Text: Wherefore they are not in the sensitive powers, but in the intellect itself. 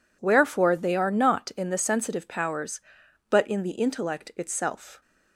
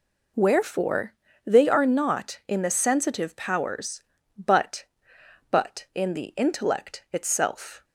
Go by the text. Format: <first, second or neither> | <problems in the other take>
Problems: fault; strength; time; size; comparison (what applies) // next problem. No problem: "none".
first | pauses between "Wherefore" and "they"; slight; at 1.1 s; 0.32 s long // says "but" twice; at 5.5 s